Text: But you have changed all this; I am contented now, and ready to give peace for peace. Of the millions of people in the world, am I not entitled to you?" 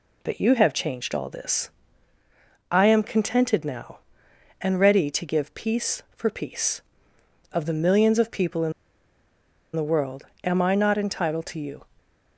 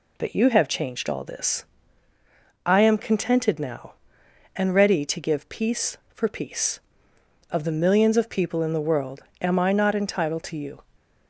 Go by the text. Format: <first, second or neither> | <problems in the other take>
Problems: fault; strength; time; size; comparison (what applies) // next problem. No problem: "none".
second | pauses between "in" and "the"; at 8.7 s; 1.0 s long